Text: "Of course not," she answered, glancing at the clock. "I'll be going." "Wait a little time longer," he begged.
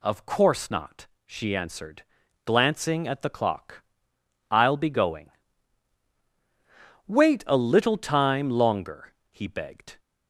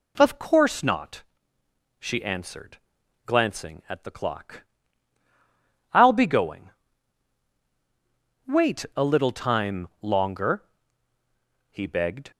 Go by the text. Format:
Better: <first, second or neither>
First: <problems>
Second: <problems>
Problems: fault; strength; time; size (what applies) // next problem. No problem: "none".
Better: neither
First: none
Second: none